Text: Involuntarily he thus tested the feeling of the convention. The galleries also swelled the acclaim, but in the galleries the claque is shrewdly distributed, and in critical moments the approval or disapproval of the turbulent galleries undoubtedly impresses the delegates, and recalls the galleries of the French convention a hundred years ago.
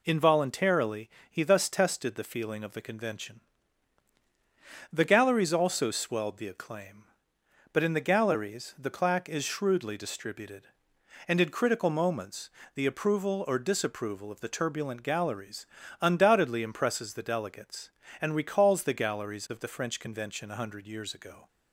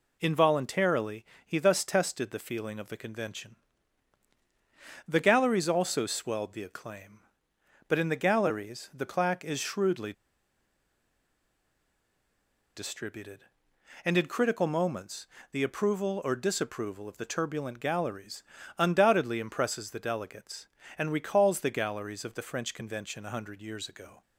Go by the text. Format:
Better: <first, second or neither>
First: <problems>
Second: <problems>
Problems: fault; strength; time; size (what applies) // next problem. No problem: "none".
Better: first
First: pauses between "Involuntarily" and "he"; slight; at 1.0 s; 0.20 s long // pauses between "moments" and "the"; slight; at 12.4 s; 0.26 s long // pauses between "galleries" and "undoubtedly"; slight; at 15.6 s; 0.34 s long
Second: pauses between "Involuntarily" and "he"; slight; at 1.2 s; 0.20 s long // pauses between "shrewdly" and "distributed"; strong; at 10.1 s; 2.6 s long // pauses between "moments" and "the"; slight; at 15.2 s; 0.26 s long // pauses between "galleries" and "undoubtedly"; slight; at 18.4 s; 0.34 s long